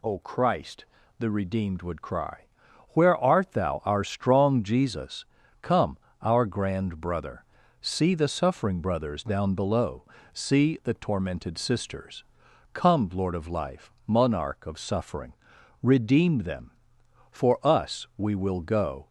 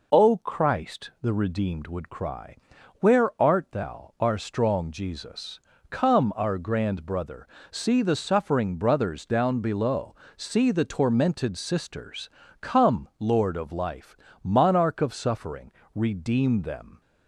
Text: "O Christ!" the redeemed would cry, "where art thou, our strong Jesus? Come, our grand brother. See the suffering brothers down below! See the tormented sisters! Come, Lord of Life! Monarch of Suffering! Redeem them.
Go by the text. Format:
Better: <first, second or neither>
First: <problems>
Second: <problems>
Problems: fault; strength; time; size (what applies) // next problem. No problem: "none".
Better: second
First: goes on to say "For us we will go"; strong; from 17.3 s on; 1.7 s long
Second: none